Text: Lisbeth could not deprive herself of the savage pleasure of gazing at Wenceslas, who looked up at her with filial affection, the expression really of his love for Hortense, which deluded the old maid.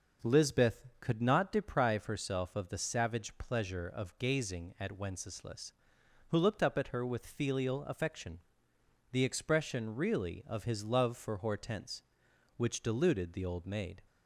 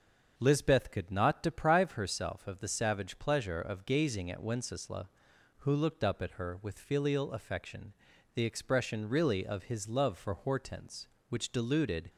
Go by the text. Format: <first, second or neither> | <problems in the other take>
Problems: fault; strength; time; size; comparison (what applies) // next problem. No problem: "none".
first | starts louder than the rest; until 1.3 s; 6.5 dB // stops before "the old maid"; at 12.0 s